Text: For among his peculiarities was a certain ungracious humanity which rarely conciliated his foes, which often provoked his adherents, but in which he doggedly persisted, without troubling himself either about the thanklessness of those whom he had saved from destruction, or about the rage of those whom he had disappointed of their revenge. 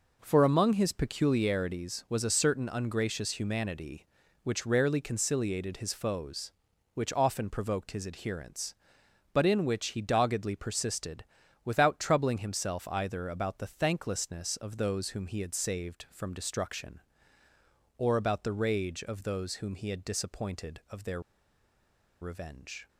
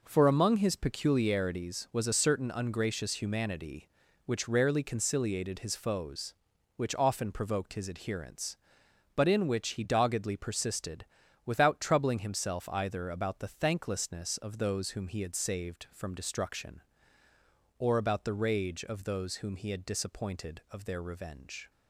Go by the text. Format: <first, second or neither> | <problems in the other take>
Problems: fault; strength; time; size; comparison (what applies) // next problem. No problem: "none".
second | pauses between "their" and "revenge"; at 21.2 s; 1.0 s long